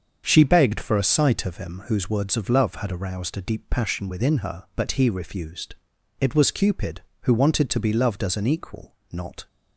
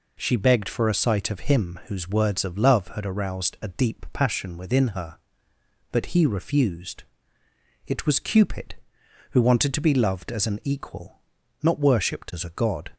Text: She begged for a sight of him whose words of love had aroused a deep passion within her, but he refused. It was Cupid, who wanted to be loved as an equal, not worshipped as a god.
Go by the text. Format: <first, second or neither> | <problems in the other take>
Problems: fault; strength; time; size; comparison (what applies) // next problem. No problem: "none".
second | starts louder than the rest; until 1.2 s; 7 dB // stops before "worshipped as a god"; at 9.4 s